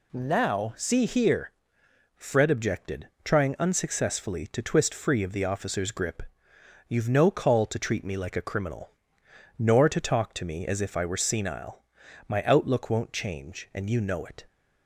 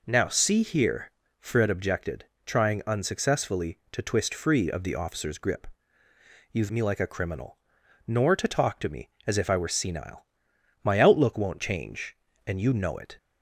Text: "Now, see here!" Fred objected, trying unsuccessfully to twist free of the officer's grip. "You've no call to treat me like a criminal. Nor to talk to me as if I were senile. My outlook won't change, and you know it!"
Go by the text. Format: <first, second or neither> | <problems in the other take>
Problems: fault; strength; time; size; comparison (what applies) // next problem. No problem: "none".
first | skips "no call to treat"; at 6.7 s